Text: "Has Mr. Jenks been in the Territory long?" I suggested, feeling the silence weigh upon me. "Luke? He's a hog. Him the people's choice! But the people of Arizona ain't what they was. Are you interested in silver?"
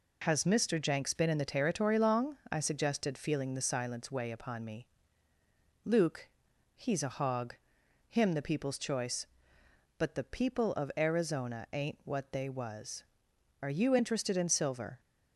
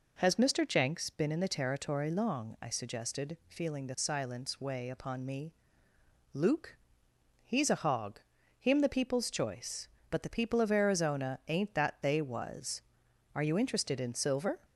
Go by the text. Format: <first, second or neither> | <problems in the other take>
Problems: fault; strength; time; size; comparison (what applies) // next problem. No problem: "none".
first | says "that" for "what"; at 11.7 s